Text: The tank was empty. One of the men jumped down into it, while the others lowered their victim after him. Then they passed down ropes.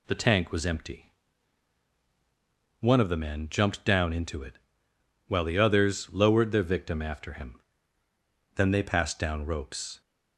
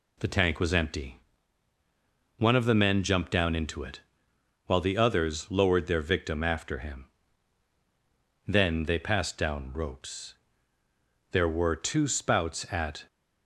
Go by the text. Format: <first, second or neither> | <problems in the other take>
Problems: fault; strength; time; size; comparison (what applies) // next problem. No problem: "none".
first | goes on to say "There were two spouts at"; strong; from 11.3 s on; 1.7 s long